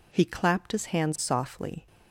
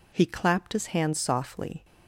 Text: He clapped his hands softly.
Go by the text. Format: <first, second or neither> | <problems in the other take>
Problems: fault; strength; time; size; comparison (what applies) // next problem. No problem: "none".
neither | none